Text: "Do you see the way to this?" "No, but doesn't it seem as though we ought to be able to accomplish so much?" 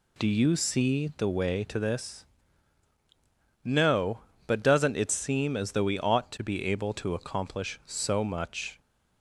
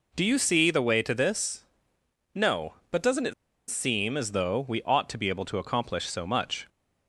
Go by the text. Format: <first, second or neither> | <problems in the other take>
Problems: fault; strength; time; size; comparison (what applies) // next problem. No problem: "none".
first | pauses between "it" and "seem"; at 3.3 s; 0.36 s long